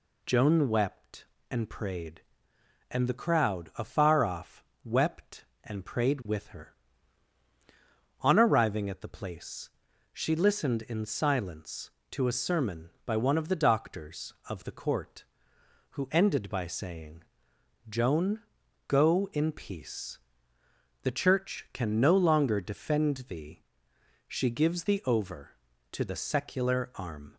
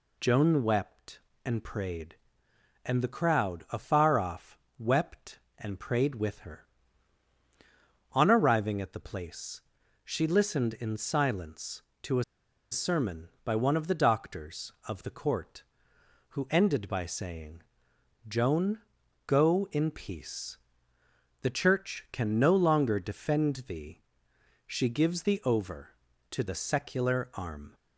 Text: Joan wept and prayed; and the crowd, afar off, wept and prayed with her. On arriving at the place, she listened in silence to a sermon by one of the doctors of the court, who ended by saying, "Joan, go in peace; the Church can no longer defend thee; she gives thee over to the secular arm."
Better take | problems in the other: first | pauses between "a" and "sermon"; noticeable; at 12.2 s; 0.48 s long

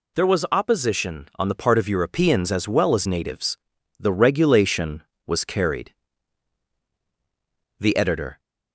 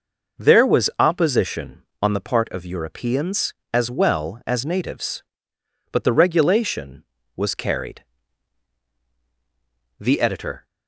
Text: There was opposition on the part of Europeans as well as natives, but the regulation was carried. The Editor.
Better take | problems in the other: second | skips "but"; at 3.7 s

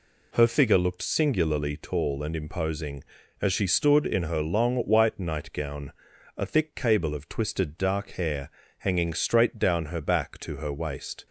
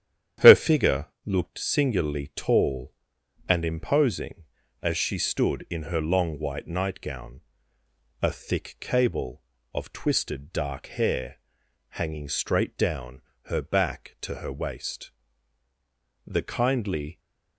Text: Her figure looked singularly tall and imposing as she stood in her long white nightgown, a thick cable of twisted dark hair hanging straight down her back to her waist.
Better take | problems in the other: first | starts louder than the rest; strong; until 1.5 s; 10 dB // pauses between "figure" and "looked"; slight; at 1.0 s; 0.18 s long // pauses between "hair" and "hanging"; noticeable; at 11.3 s; 0.50 s long; slight in the first // pauses between "down" and "her"; slight; at 13.2 s; 0.26 s long // goes on to say "The kindly"; noticeable; from 16.2 s on; 0.94 s long

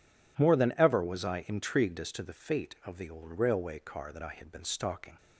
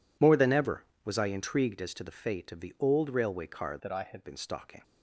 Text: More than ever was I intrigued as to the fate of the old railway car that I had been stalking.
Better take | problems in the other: first | changes voice from "that" to "had"; from 3.8 to 4.2 s; 0.4 s long

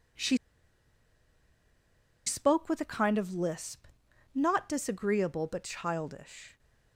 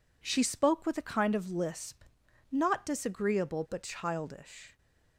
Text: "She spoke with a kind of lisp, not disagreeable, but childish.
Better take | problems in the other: second | pauses between "She" and "spoke"; strong; at 0.3 s; 1.8 s long

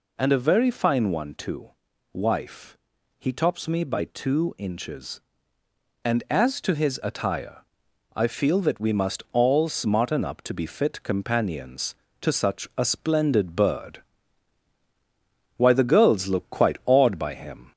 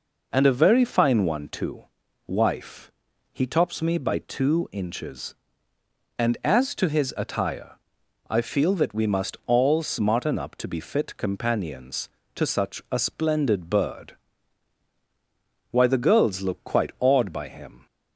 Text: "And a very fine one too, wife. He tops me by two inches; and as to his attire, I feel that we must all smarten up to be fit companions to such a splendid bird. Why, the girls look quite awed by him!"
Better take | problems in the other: second | gets louder; slight; throughout; 2 dB

